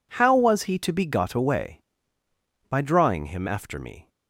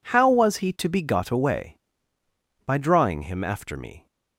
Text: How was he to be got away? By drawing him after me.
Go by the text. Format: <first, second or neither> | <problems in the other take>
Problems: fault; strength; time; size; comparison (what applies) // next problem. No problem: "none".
neither | none